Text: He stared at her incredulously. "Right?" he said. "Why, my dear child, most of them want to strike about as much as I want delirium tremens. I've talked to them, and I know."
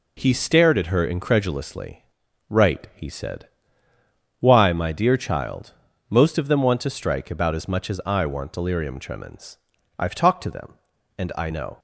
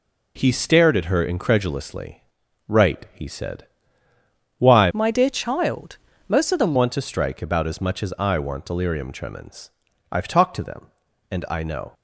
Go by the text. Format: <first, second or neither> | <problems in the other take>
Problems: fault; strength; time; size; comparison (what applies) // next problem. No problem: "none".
first | changes voice from "my" to "them"; from 4.9 to 6.7 s; 1.8 s long